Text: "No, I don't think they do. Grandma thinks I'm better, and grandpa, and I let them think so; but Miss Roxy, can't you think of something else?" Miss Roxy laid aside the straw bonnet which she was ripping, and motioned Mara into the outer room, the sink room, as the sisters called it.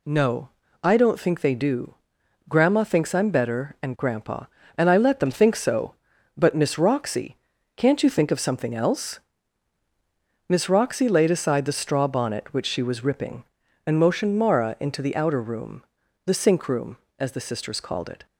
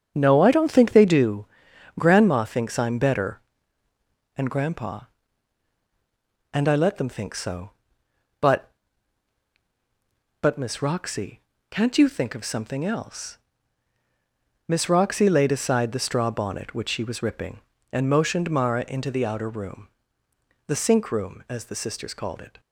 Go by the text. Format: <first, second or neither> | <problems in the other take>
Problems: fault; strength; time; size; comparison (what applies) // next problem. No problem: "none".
first | starts louder than the rest; strong; until 1.1 s; 7.5 dB // says "but" twice; at 10.3 s